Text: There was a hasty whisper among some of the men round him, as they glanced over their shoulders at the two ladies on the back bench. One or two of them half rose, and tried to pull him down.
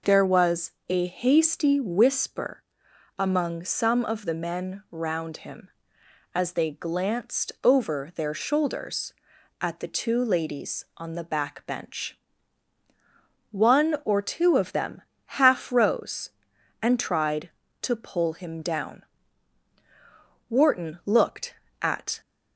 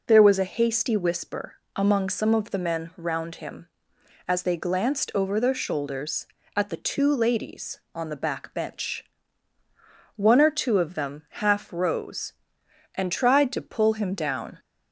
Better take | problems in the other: second | pauses between "was" and "a"; slight; at 0.7 s; 0.18 s long // pauses between "whisper" and "among"; noticeable; at 2.6 s; 0.56 s long; slight in the second // pauses between "them" and "half"; at 15.0 s; 0.40 s long // goes on to say "Wharton looked at"; strong; from 20.5 s on; 1.7 s long

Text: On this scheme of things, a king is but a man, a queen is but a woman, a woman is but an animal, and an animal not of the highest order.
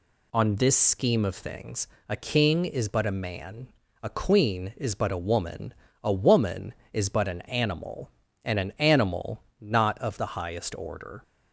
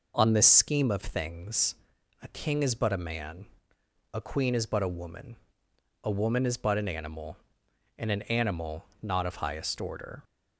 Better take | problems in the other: first | pauses between "animal" and "not"; slight; at 8.8 s; 0.16 s long; slight in the first // skips "the"; at 9.3 s

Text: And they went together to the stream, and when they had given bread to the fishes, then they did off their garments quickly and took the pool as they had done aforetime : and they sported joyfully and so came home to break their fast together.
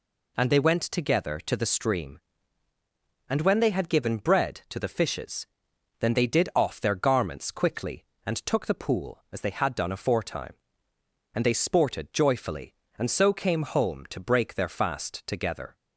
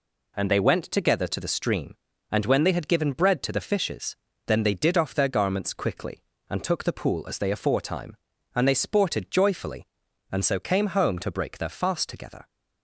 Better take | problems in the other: first | skips "had done"; at 7.5 s

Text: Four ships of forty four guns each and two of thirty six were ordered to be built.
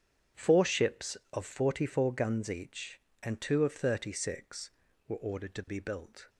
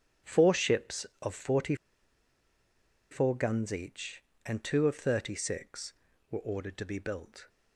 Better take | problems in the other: first | starts louder than the rest; strong; until 1.4 s; 8.5 dB; strong in the first // pauses between "forty" and "four"; strong; at 1.7 s; 1.3 s long

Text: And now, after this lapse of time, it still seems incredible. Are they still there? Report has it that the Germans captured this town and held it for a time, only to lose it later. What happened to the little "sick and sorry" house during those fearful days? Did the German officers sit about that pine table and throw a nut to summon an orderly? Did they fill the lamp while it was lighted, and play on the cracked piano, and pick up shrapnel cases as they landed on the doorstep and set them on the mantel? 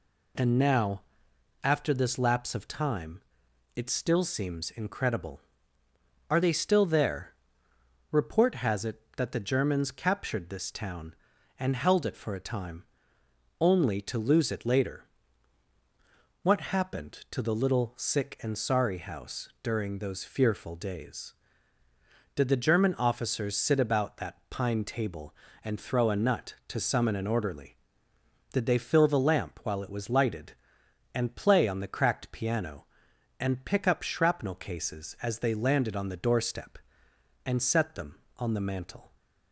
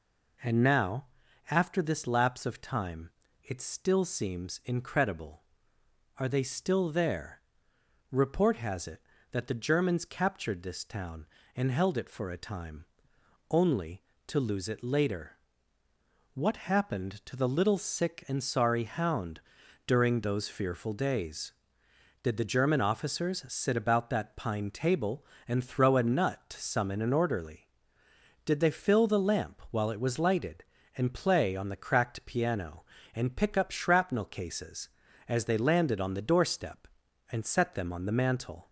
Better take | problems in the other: first | says "hound" for "house"; at 18.8 s

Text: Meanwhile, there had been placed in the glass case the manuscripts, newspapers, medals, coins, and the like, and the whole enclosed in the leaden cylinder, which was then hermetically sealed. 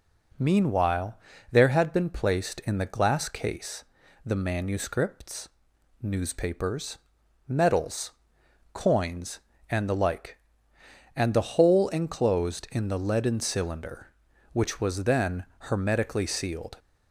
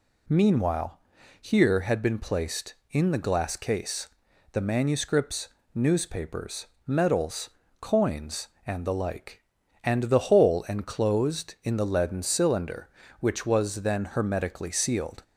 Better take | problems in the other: first | says "here" for "there"; at 1.4 s // pauses between "case" and "the"; at 4.0 s; 0.42 s long; also in the first

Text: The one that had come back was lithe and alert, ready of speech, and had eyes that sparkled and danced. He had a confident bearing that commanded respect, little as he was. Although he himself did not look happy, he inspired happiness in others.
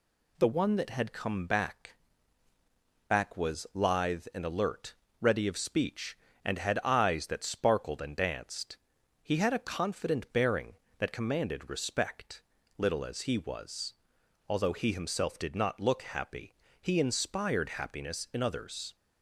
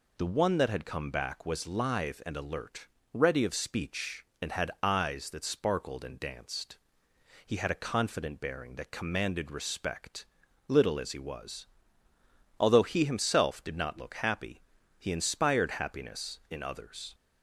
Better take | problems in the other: second | says "back" twice; at 3.0 s

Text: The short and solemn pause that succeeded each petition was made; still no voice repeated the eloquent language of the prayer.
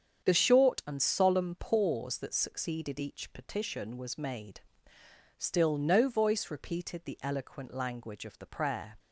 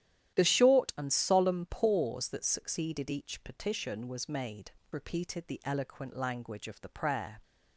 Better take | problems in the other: first | starts louder than the rest; strong; until 1.3 s; 11.5 dB; strong in the first // skips "still no voice"; at 4.8 s

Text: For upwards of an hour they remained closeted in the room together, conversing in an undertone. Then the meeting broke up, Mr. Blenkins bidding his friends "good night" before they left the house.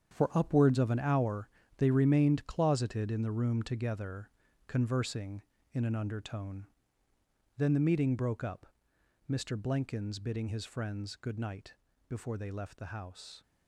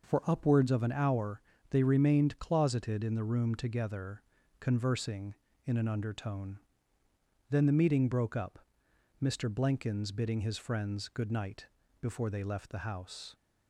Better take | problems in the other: second | gets quieter; strong; throughout; 11 dB // pauses between "hour" and "they"; slight; at 1.4 s; 0.30 s long; slight in the second // pauses between "night" and "before"; slight; at 11.7 s; 0.36 s long; slight in the second

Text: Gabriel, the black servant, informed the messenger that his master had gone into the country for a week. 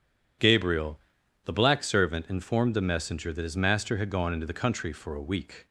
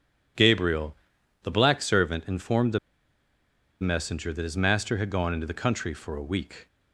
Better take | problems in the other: first | pauses between "the" and "messenger"; at 2.7 s; 1.0 s long

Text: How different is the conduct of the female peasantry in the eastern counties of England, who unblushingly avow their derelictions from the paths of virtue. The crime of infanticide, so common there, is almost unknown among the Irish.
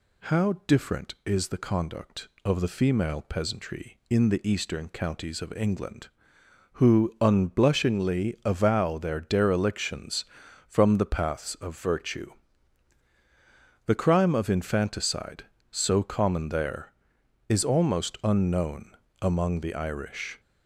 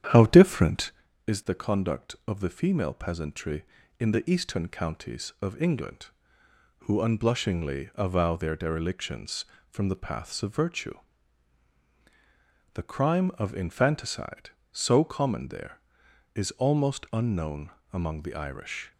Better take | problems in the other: first | starts louder than the rest; strong; until 1.1 s; 9.5 dB // pauses between "unknown" and "among"; slight; at 17.6 s; 0.22 s long; slight in the first

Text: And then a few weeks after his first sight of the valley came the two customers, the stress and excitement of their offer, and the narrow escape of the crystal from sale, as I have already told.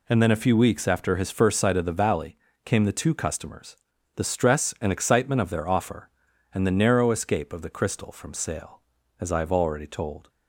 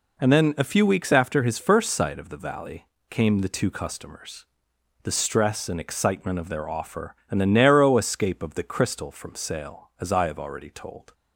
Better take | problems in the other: neither | pauses between "valley" and "came"; slight; the same in both

